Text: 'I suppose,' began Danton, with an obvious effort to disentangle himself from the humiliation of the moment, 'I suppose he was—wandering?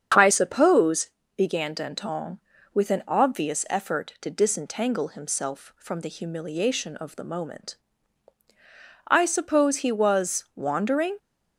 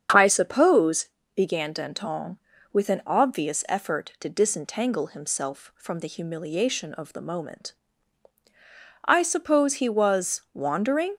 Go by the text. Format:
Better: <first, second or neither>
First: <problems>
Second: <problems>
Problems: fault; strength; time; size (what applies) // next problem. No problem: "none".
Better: neither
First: starts louder than the rest; strong; until 1.4 s; 7.5 dB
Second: starts louder than the rest; strong; until 1.3 s; 7.5 dB